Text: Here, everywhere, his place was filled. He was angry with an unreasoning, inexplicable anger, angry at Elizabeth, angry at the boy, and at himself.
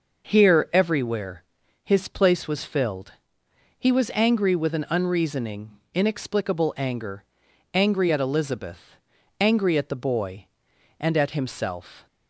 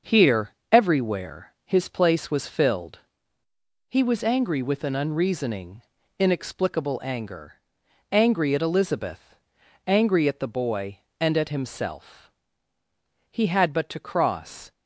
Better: first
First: none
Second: starts louder than the rest; until 1.2 s; 6.5 dB // goes on to say "He had but to cross"; from 13.3 s on; 1.4 s long

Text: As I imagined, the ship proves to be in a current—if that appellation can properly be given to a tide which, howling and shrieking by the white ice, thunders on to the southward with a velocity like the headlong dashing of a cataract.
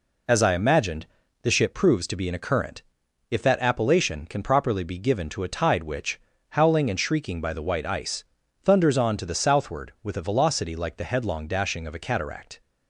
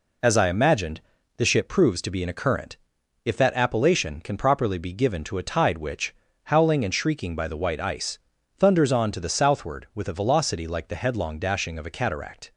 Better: neither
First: none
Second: none

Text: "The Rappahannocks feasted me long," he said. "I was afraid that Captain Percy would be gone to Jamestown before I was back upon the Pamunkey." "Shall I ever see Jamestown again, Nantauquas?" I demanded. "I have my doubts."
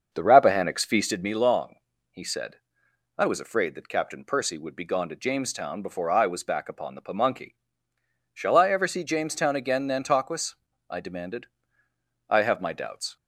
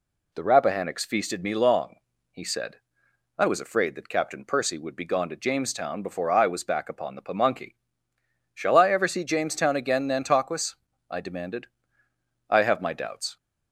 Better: second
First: starts louder than the rest; until 1.3 s; 6.5 dB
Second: none

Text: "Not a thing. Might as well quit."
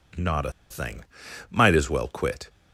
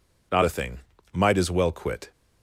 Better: second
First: pauses between "a" and "thing"; slight; at 0.5 s; 0.18 s long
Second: none

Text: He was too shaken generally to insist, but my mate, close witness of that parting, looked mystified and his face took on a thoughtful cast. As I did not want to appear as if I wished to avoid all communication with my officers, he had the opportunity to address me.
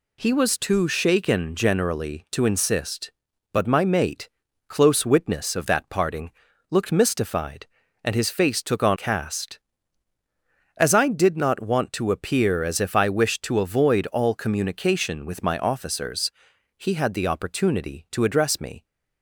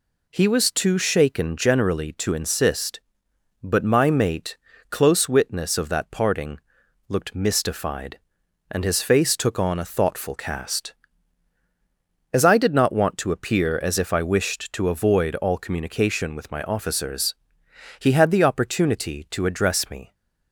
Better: second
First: skips "a thoughtful"; at 8.9 s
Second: none

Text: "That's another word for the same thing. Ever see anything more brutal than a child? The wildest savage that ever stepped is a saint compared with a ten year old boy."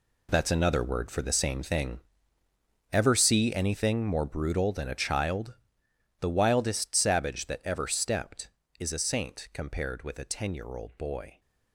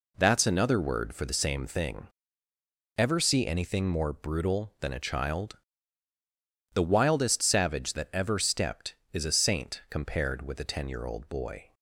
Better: second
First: gets quieter; strong; throughout; 12 dB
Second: none

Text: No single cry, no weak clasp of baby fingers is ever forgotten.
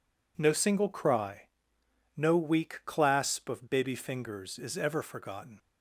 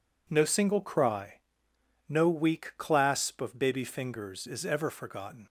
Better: neither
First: none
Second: none

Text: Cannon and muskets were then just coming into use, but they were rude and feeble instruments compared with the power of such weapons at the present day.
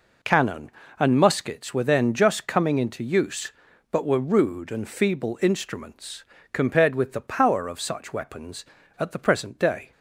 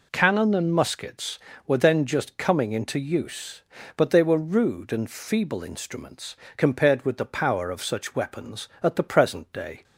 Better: second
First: skips "they"; at 4.0 s // pauses between "instruments" and "compared"; slight; at 6.2 s; 0.28 s long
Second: pauses between "instruments" and "compared"; slight; at 6.3 s; 0.23 s long

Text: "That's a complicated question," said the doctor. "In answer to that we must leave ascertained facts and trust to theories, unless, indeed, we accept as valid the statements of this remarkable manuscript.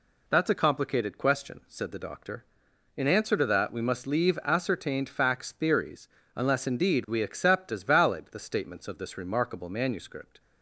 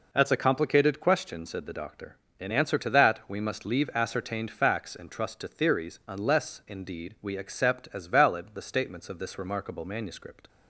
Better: second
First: skips "and trust to"; at 5.5 s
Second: none

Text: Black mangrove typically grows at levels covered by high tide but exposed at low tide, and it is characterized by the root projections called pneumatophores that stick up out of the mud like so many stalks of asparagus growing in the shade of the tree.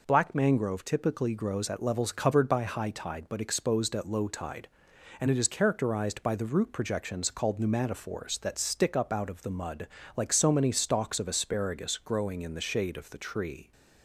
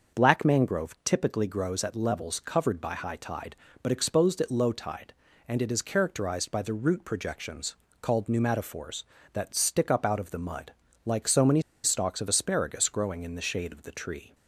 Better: first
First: pauses between "mud" and "like"; slight; at 9.8 s; 0.28 s long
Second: starts louder than the rest; until 1.2 s; 6.5 dB // pauses between "projections" and "called"; slight; at 7.7 s; 0.26 s long // pauses between "mud" and "like"; slight; at 10.7 s; 0.32 s long // pauses between "many" and "stalks"; slight; at 11.6 s; 0.22 s long

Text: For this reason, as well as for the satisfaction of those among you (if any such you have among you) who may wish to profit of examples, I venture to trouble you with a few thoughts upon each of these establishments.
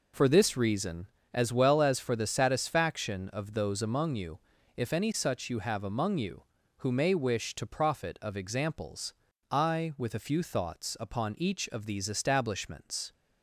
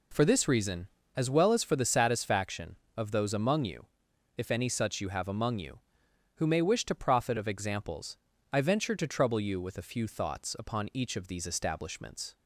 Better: second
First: skips "venture to trouble you"; at 9.9 s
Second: none

